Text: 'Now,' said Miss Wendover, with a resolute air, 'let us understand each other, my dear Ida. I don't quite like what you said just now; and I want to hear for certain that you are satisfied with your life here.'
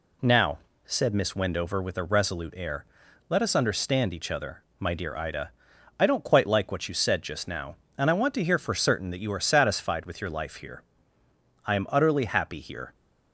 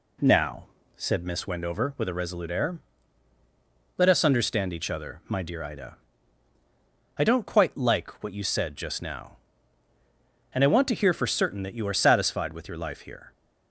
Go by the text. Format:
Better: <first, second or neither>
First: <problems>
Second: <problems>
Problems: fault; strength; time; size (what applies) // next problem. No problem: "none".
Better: second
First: goes on to say "I am utterly happy here"; noticeable; from 11.6 s on; 1.2 s long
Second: none